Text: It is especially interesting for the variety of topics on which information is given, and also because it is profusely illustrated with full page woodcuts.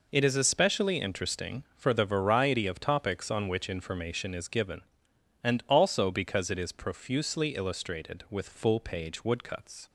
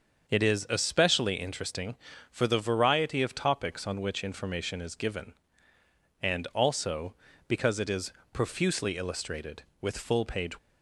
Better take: first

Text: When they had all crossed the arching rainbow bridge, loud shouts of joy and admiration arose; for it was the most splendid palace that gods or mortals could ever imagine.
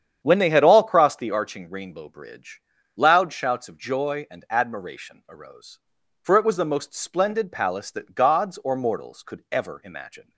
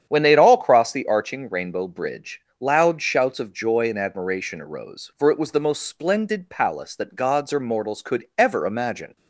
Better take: neither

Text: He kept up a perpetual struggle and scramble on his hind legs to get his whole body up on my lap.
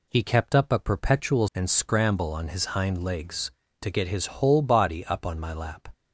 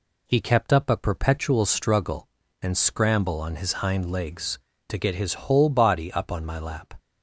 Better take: second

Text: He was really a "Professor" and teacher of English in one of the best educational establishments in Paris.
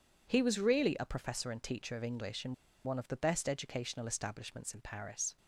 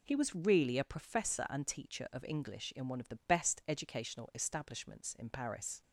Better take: second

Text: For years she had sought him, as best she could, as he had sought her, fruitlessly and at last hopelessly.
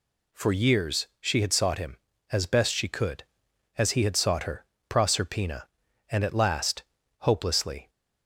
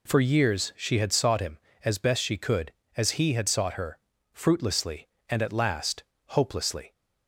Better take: second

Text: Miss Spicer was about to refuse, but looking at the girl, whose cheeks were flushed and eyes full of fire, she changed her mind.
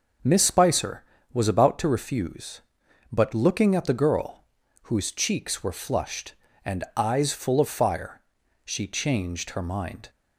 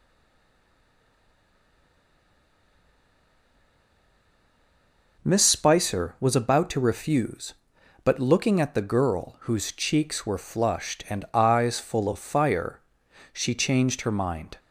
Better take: first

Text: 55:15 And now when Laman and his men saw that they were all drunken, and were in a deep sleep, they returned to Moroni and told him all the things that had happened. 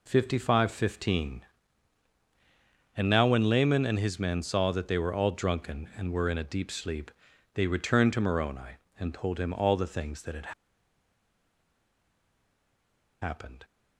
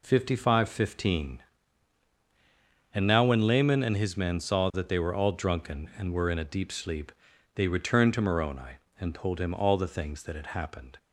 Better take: second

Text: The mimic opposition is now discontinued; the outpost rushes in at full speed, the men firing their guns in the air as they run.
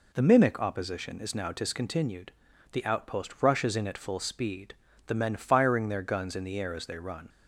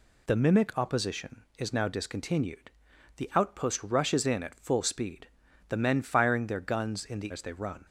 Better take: first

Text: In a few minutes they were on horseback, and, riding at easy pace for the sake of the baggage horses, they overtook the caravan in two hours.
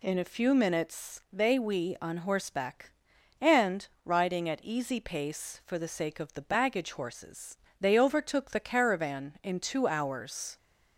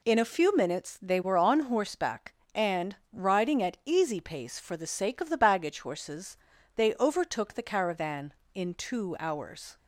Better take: second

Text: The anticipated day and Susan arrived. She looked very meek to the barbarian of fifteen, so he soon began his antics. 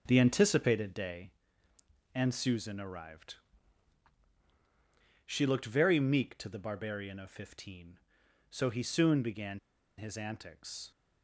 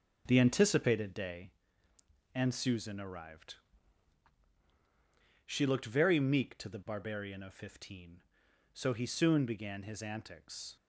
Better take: second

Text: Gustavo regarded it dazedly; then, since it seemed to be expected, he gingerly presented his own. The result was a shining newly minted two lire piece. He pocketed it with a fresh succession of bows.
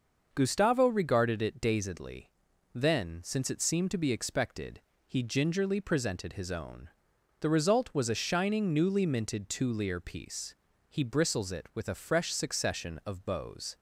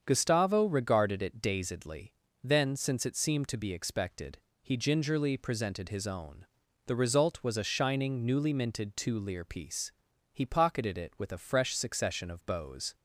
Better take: second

